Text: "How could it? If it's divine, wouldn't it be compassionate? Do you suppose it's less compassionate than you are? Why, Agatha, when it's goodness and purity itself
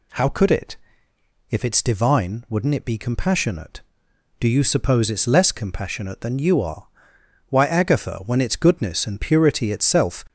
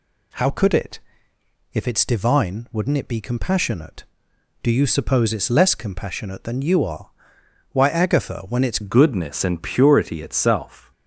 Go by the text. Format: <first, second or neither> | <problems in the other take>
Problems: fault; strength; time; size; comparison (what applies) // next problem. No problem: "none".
first | changes voice at "goodness"; from 8.8 s on; 2.1 s long